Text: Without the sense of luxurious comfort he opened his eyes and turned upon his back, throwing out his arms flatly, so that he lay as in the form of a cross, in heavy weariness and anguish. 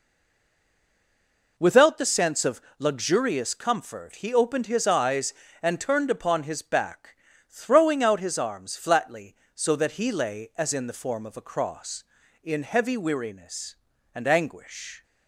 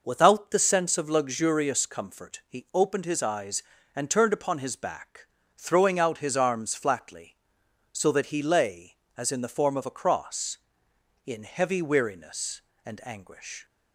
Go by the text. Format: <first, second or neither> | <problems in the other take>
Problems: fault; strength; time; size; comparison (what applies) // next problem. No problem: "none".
second | stays silent before the first word; noticeable; until 1.5 s; 1.5 s long // pauses between "of" and "luxurious"; slight; at 2.6 s; 0.16 s long